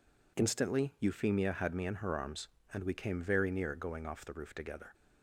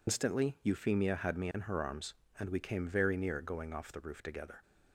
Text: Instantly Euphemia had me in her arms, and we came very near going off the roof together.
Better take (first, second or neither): first